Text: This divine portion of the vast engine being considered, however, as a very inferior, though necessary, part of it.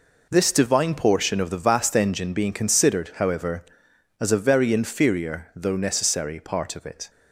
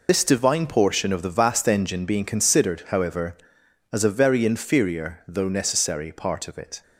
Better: first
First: none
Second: loses the start of "This"; at 0.0 s; 70 ms

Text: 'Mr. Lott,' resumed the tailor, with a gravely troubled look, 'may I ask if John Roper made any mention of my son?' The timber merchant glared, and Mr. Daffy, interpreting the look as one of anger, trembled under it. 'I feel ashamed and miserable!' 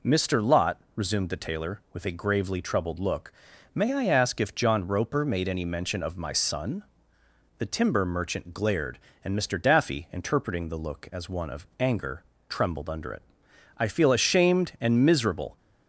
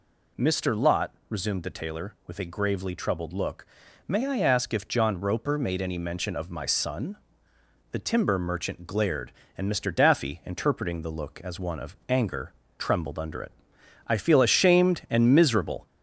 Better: first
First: none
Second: gets louder; slight; throughout; 2.5 dB

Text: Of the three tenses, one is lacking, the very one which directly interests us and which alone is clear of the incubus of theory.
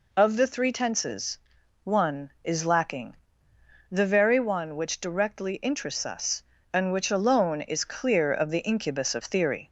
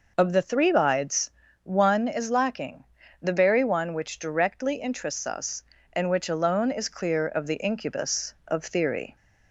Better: first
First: none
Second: says "bides" for "tenses"; at 0.7 s

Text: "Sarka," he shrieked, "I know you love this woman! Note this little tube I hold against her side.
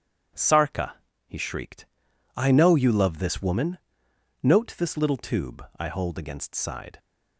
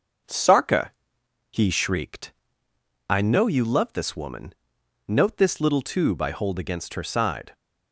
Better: second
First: skips "her"; at 6.5 s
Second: none

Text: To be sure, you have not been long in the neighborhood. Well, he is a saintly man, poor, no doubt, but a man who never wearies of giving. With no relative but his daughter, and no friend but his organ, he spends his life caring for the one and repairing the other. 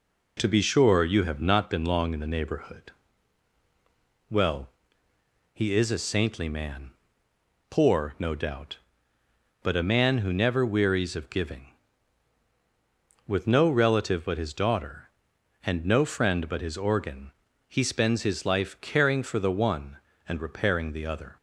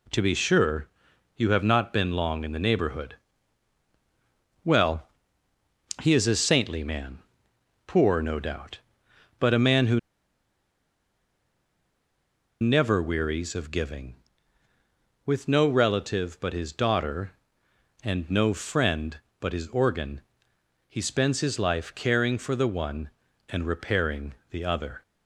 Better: first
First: none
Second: pauses between "who" and "never"; strong; at 9.9 s; 2.6 s long // pauses between "repairing" and "the"; slight; at 24.3 s; 0.16 s long

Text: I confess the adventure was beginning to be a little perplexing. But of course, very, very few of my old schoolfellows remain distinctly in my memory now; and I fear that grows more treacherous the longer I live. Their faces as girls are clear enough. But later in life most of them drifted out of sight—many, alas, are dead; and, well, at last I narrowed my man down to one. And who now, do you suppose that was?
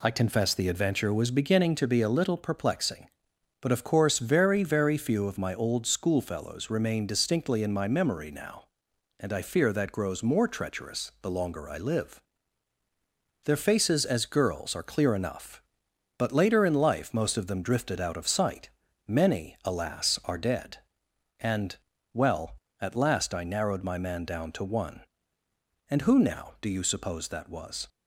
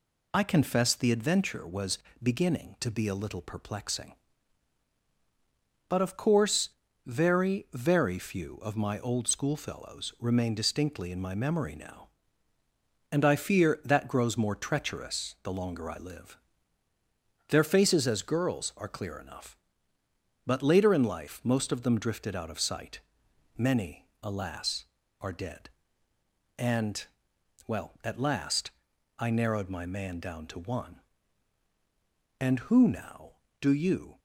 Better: first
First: none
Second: pauses between "was" and "beginning"; slight; at 1.9 s; 0.24 s long // pauses between "last" and "I"; noticeable; at 28.6 s; 0.52 s long // stops before "suppose that was"; at 34.1 s

